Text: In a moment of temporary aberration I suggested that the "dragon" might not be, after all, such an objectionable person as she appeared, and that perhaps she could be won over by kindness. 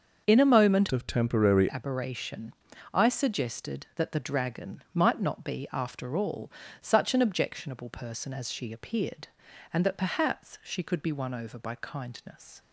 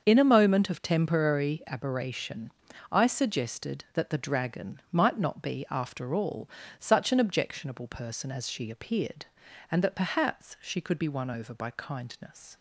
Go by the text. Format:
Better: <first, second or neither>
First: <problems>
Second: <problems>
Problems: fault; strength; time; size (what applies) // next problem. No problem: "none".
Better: second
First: starts louder than the rest; until 1.2 s; 6.5 dB // changes voice from "of" to "temporary"; from 0.9 to 1.6 s; 0.7 s long // pauses between "aberration" and "I"; at 2.5 s; 0.38 s long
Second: starts louder than the rest; until 1.0 s; 6.5 dB // pauses between "aberration" and "I"; at 2.5 s; 0.38 s long